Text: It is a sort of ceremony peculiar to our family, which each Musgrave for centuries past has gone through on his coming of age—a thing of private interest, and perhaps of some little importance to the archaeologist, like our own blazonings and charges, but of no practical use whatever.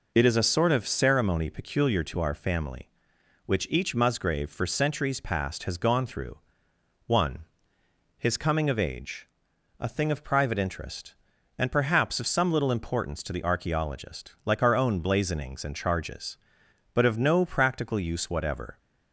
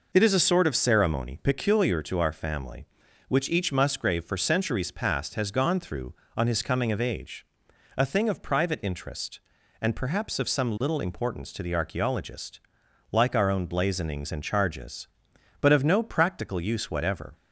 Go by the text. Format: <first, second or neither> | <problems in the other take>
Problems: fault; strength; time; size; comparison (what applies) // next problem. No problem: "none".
second | says "one" for "on"; at 7.0 s